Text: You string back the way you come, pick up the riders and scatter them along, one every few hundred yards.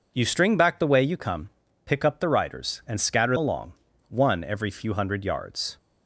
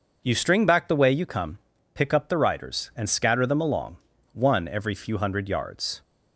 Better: second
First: skips "them"; at 3.3 s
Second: none

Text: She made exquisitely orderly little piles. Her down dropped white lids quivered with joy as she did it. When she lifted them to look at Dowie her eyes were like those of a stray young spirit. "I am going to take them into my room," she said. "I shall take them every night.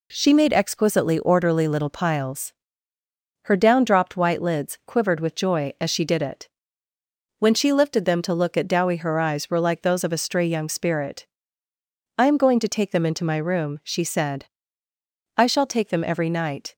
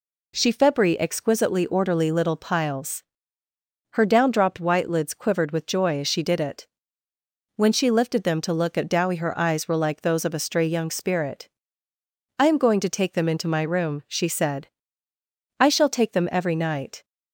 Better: first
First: none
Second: says "febri" for "made"; at 0.5 s

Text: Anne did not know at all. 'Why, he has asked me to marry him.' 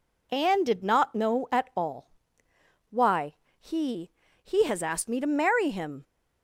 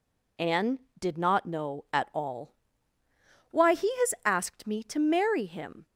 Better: second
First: says "he" twice; at 4.4 s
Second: none

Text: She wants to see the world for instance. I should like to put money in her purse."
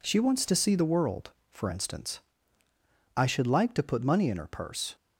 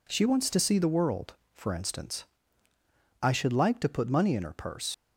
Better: first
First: none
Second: leaves "purse" unfinished; at 4.9 s; 65 ms

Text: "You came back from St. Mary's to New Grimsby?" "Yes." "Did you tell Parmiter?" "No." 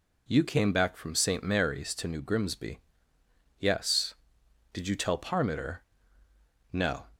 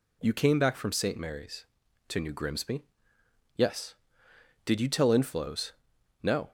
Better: first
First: none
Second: says "Inflows" for "Parmiter"; at 5.0 s

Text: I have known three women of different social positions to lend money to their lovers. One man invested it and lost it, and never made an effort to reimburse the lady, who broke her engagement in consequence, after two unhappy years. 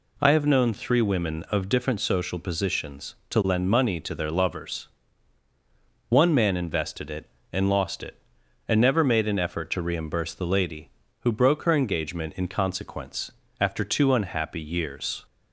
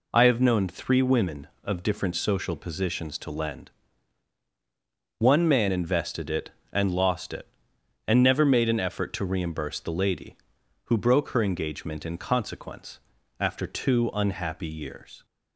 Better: first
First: none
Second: skips "money to their lovers"; at 4.4 s

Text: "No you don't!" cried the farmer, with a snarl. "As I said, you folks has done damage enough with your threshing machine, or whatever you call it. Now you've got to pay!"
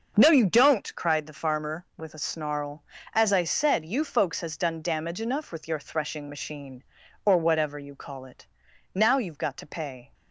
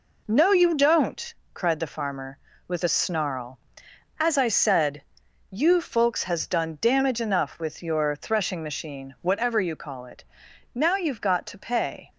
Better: first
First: none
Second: skips "or"; at 9.1 s

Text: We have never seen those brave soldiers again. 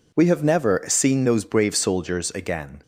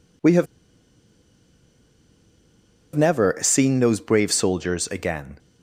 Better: first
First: none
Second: pauses between "have" and "never"; strong; at 0.4 s; 2.5 s long

